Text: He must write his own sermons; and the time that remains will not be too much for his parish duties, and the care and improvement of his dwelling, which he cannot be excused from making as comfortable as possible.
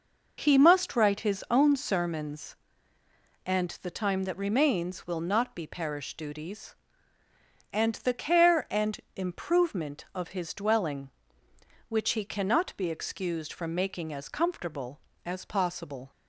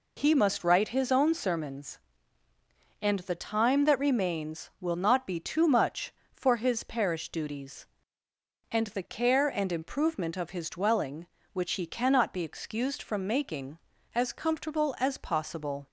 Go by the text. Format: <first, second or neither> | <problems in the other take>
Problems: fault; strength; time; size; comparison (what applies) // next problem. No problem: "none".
second | skips "too much for his"; at 5.6 s // pauses between "and" and "improvement"; slight; at 8.9 s; 0.16 s long